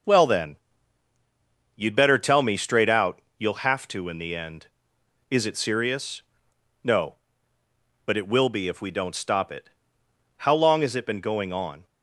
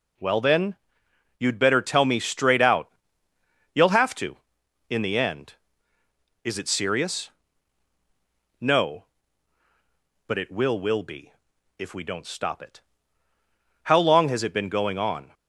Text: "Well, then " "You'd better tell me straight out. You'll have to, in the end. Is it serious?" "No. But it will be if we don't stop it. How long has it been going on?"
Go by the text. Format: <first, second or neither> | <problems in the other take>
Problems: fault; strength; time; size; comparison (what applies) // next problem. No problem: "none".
first | says "will" twice; at 10.7 s // pauses between "be" and "if"; at 11.3 s; 0.44 s long